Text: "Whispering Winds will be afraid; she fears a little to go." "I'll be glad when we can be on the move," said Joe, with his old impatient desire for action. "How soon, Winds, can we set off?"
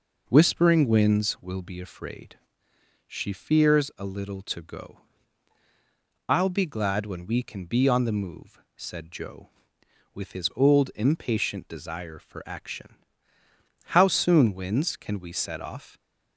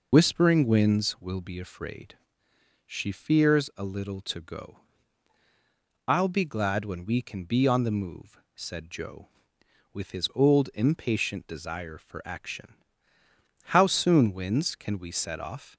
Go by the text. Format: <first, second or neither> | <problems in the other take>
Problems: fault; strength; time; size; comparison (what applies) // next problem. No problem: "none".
first | loses the start of "Whispering"; at 0.1 s; 60 ms